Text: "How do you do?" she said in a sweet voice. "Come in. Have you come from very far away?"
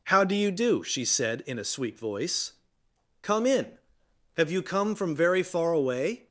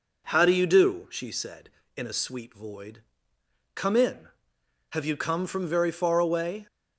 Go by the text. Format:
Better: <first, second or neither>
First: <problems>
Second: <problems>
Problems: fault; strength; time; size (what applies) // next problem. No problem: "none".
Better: first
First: none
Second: says "void" for "voice"; at 2.5 s